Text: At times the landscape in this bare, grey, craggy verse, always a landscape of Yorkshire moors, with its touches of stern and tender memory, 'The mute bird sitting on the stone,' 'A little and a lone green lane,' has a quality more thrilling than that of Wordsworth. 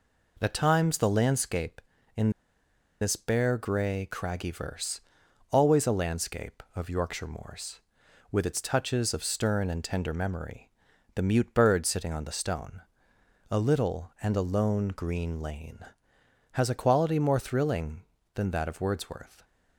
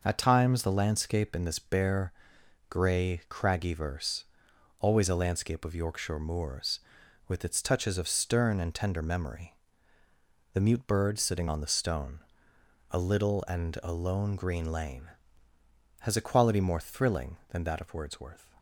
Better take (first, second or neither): second